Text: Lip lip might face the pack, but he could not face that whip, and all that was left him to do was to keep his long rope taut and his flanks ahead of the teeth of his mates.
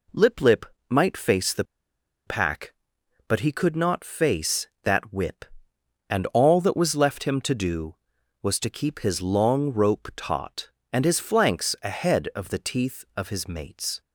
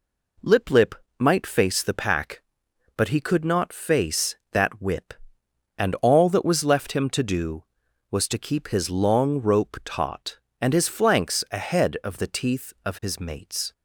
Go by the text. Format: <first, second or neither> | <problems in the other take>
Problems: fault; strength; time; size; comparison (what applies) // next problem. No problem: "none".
second | pauses between "lip" and "might"; slight; at 0.6 s; 0.24 s long; slight in the second // pauses between "the" and "pack"; noticeable; at 1.6 s; 0.63 s long